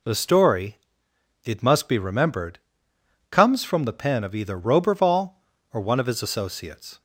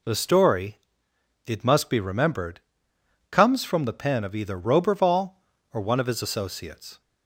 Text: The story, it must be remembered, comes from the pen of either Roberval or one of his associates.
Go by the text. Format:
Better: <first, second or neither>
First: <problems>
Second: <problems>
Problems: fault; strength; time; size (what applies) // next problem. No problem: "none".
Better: neither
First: none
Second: none